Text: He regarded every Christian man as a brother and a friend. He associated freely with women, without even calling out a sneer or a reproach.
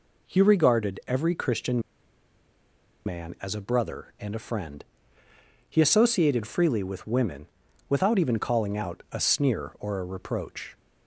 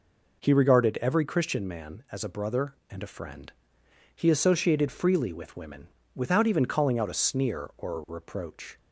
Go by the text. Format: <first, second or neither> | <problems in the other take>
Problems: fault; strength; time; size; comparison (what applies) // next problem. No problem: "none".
second | pauses between "Christian" and "man"; strong; at 1.8 s; 1.2 s long